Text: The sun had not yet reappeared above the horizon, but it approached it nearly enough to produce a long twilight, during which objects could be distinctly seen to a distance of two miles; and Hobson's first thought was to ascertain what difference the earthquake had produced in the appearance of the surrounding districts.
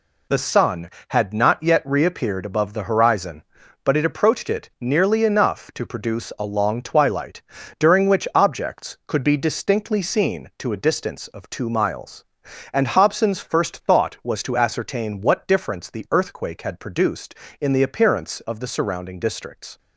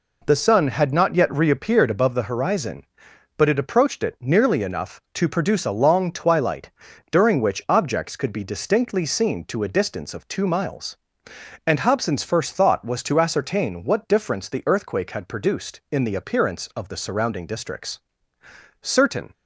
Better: first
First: none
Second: goes on to say "Certain"; from 18.8 s on; 0.52 s long

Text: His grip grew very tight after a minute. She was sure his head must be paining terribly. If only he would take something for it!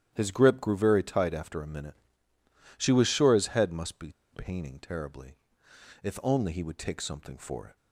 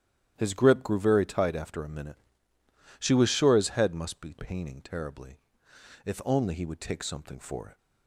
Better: second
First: starts louder than the rest; strong; until 1.1 s; 10.5 dB // pauses between "be" and "paining"; slight; at 4.1 s; 0.20 s long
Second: starts louder than the rest; strong; until 1.3 s; 10.5 dB

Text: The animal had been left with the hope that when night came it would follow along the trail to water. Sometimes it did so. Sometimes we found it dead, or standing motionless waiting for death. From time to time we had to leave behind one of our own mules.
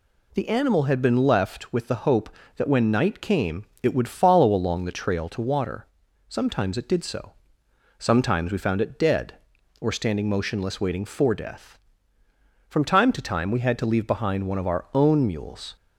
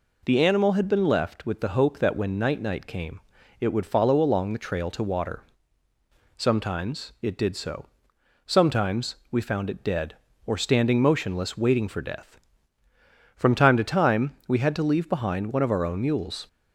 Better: first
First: pauses between "came" and "it"; slight; at 3.6 s; 0.16 s long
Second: says "night" twice; at 2.5 s // pauses between "came" and "it"; at 3.1 s; 0.40 s long

